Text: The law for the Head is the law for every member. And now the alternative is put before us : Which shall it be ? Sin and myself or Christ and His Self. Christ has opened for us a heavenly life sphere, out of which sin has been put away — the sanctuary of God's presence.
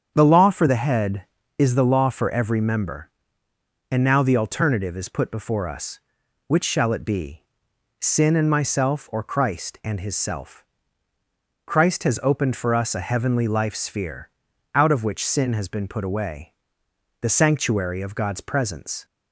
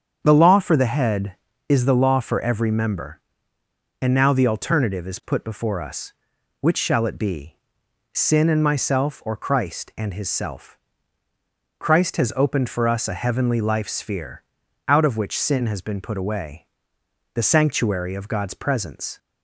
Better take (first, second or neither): neither